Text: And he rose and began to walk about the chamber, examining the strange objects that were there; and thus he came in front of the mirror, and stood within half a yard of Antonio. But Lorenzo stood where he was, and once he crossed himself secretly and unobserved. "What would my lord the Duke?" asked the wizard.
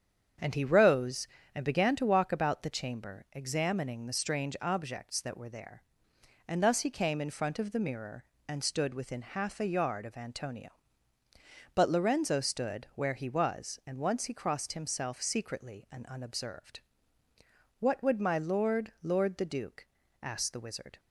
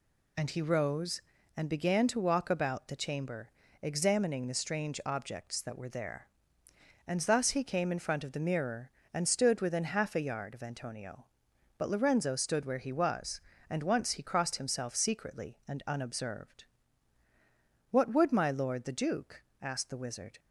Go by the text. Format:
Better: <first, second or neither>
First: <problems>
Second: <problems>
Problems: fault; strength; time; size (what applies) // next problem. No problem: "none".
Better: second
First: starts louder than the rest; strong; until 1.6 s; 8 dB // says "lord" twice; at 19.0 s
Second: none